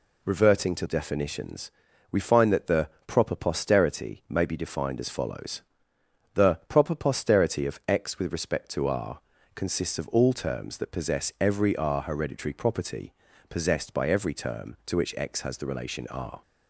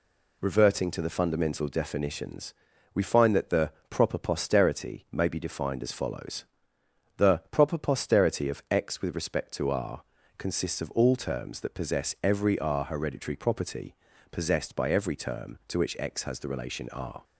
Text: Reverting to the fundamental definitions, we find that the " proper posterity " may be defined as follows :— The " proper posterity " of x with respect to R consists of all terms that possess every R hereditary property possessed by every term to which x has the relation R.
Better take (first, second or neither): second